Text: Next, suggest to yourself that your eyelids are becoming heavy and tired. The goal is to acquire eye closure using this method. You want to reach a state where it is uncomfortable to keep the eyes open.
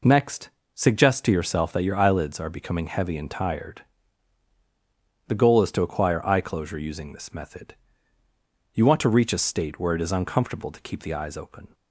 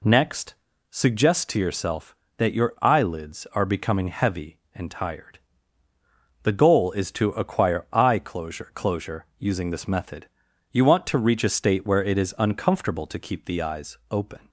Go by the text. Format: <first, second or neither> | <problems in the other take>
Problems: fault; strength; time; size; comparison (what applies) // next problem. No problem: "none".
first | says "closure" twice; at 8.7 s